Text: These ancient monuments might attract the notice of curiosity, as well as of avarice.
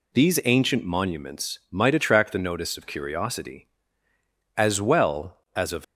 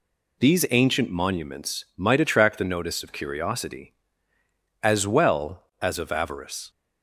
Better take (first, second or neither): second